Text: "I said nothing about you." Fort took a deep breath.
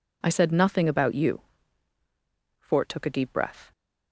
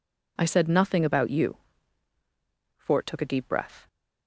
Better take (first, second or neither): neither